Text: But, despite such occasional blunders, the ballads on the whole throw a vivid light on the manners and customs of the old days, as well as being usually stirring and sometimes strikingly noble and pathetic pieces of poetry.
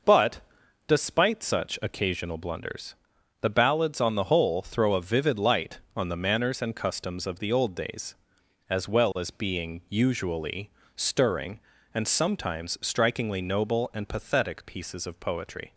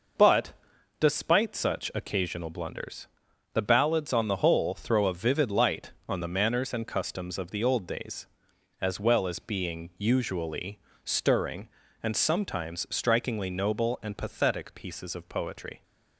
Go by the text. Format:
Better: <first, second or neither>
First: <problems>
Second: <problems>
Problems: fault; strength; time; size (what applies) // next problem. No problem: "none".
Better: neither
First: pauses between "usually" and "stirring"; slight; at 10.6 s; 0.26 s long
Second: pauses between "usually" and "stirring"; slight; at 10.7 s; 0.26 s long